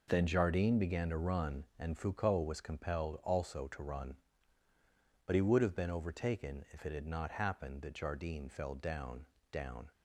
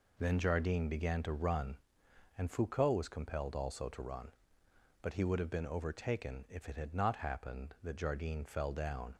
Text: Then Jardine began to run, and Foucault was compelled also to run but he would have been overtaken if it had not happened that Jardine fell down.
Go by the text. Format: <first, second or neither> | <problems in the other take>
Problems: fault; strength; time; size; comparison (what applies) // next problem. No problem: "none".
second | says "down" twice; at 9.5 s